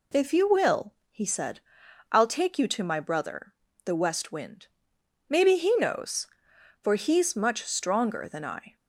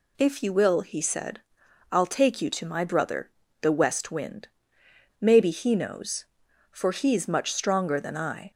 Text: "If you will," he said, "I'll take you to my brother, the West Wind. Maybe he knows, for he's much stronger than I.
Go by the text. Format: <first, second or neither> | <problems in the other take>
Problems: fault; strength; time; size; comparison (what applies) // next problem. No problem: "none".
neither | none